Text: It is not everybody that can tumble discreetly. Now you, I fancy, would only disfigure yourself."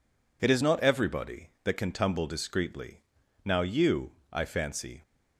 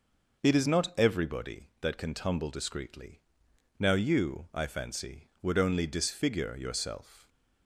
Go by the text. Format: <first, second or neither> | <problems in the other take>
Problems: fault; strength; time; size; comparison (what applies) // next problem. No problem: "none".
second | stops before "would only disfigure yourself"; at 5.0 s